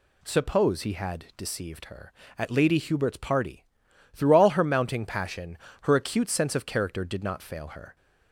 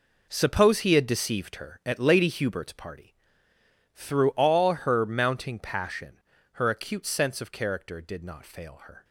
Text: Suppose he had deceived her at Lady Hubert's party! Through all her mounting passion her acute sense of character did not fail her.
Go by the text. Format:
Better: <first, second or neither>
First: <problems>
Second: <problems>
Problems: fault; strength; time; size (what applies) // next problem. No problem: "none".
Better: first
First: pauses between "passion" and "her"; slight; at 5.5 s; 0.24 s long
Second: gets quieter; strong; throughout; 11.5 dB // pauses between "passion" and "her"; slight; at 6.2 s; 0.32 s long